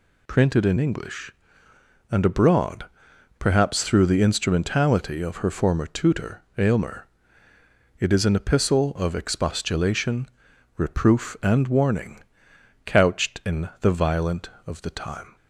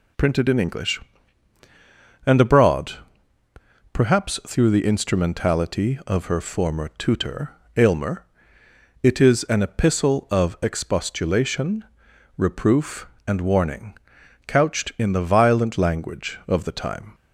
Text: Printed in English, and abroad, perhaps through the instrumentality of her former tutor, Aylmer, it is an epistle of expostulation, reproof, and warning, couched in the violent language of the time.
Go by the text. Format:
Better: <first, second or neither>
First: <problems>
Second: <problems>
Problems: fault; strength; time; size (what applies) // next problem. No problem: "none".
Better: second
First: skips "language"; at 14.5 s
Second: none